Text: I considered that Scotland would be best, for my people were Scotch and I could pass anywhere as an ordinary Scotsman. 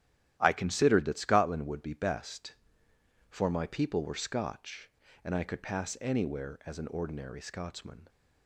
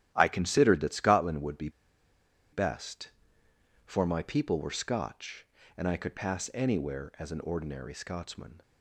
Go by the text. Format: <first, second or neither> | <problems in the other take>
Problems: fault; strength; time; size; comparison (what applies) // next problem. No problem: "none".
first | starts louder than the rest; strong; until 1.1 s; 12 dB; strong in the first // pauses between "be" and "best"; noticeable; at 1.6 s; 0.83 s long